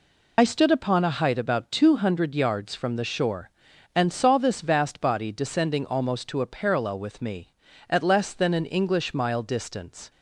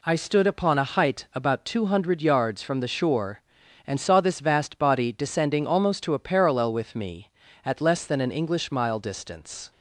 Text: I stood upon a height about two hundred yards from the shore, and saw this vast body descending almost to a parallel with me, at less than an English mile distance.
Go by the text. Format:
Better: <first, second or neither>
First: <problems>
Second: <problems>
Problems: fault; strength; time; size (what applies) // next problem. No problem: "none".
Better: second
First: loses the start of "I"; at 0.3 s; 40 ms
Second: none